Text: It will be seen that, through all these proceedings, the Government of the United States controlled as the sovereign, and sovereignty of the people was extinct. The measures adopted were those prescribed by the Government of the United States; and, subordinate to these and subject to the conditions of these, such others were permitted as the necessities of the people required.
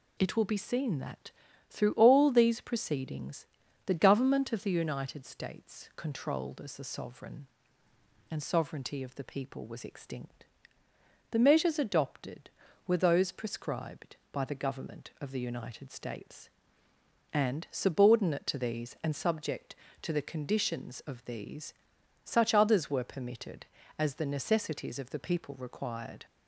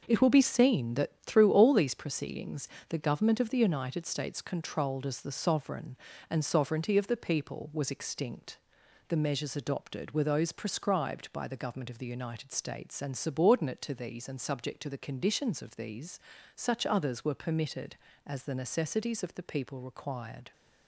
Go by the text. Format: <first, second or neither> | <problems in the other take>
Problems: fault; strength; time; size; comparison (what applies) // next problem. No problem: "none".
neither | none